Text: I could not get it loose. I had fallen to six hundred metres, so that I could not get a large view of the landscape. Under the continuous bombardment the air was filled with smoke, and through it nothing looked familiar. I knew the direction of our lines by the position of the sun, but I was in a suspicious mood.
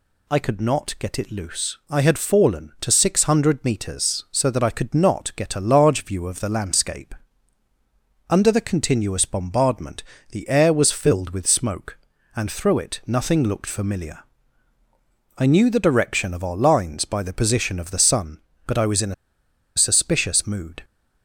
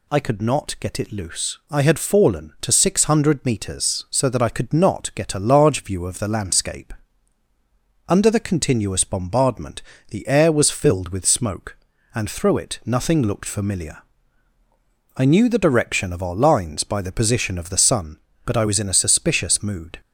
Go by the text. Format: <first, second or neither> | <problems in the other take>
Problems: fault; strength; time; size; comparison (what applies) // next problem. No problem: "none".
second | pauses between "bombardment" and "the"; slight; at 10.0 s; 0.28 s long; slight in the second // pauses between "a" and "suspicious"; noticeable; at 19.1 s; 0.63 s long